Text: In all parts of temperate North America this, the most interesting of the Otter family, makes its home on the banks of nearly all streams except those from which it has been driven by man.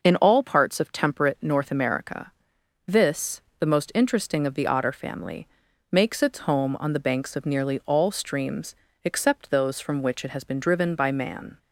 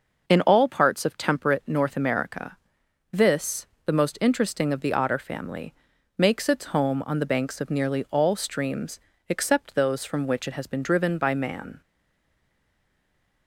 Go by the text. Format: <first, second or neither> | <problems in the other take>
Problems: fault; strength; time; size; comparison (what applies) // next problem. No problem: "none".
first | pauses between "America" and "this"; noticeable; at 2.5 s; 0.56 s long; noticeable in the first // pauses between "streams" and "except"; slight; at 8.9 s; 0.30 s long; slight in the first // stays silent after the last word; noticeable; from 11.8 s on; 1.6 s long